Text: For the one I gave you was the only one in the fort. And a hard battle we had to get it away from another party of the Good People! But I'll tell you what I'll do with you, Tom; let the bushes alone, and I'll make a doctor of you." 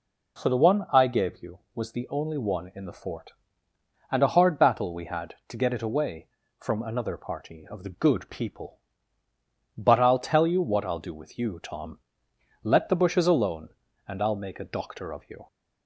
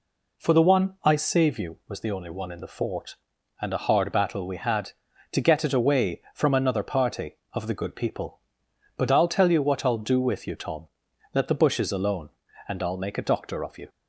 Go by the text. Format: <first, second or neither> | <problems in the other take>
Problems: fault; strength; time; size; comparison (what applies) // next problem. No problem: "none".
first | says "save" for "gave"; at 1.1 s